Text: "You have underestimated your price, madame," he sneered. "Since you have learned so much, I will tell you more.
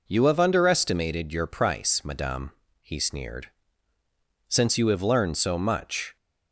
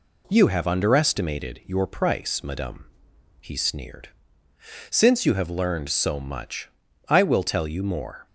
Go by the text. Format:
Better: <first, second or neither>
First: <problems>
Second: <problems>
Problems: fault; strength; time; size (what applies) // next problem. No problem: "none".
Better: second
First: stops before "I will tell you more"; at 6.1 s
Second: none